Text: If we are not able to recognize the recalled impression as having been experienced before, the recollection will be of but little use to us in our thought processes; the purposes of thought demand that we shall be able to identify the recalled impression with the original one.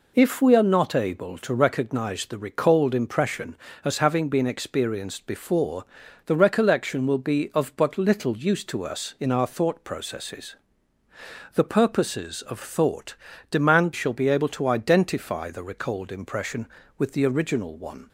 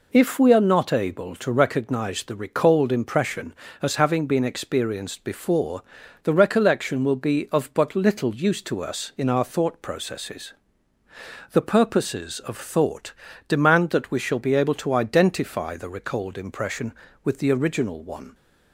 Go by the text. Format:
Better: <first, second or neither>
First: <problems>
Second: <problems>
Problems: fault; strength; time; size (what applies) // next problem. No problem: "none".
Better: second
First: pauses between "thought" and "demand"; slight; at 13.1 s; 0.34 s long // skips "that we"; at 13.9 s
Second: pauses between "thought" and "demand"; slight; at 13.1 s; 0.34 s long